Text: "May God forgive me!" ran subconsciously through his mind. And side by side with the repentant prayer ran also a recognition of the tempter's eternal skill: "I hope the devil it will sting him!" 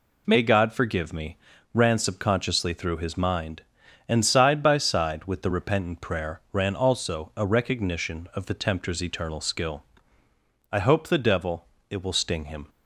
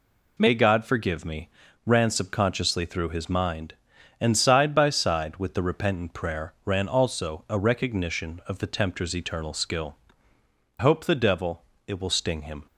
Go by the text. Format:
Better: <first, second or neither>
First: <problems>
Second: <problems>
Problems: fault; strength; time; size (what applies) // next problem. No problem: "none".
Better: first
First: pauses between "devil" and "it"; slight; at 11.6 s; 0.24 s long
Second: skips "I"; at 10.3 s // pauses between "devil" and "it"; slight; at 11.6 s; 0.24 s long